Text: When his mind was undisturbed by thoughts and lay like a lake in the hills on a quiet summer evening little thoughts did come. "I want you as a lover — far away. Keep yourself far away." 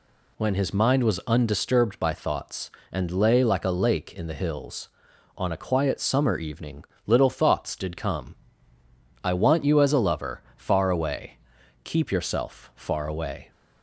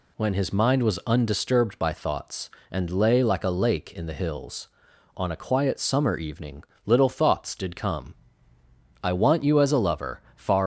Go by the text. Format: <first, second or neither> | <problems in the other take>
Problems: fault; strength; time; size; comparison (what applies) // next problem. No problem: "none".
first | pauses between "evening" and "little"; slight; at 6.6 s; 0.24 s long; slight in the first // stops before "away Keep yourself far away"; at 10.6 s